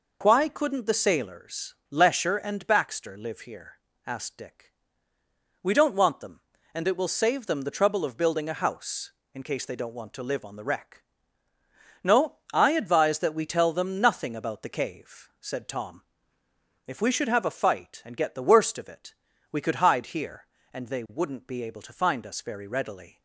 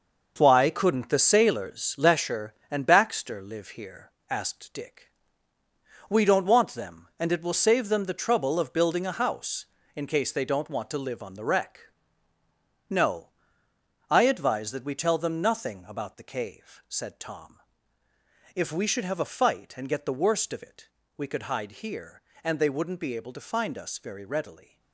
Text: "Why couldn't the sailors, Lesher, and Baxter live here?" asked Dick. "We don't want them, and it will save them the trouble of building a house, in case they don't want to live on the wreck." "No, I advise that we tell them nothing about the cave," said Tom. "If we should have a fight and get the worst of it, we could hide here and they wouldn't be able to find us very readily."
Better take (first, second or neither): first